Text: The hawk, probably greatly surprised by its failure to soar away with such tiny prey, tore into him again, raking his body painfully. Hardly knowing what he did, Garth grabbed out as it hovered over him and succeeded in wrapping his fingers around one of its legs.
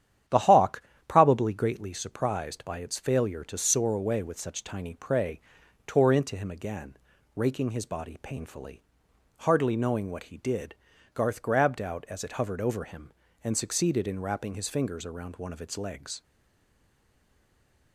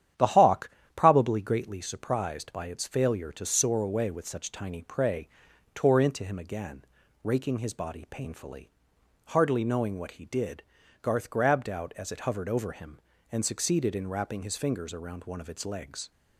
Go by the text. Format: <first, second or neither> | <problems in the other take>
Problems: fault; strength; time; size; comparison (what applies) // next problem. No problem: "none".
second | starts louder than the rest; strong; until 1.5 s; 10 dB; strong in the second // stays silent after the last word; noticeable; from 16.2 s on; 1.7 s long